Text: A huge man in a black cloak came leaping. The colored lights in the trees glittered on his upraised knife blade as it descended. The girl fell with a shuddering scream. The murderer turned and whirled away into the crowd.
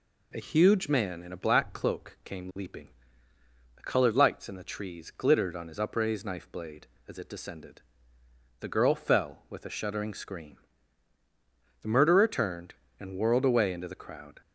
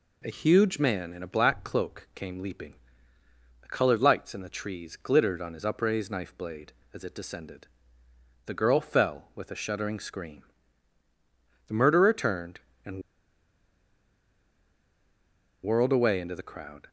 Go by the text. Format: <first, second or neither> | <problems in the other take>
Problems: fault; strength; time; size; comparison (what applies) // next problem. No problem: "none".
first | pauses between "and" and "whirled"; strong; at 13.0 s; 2.6 s long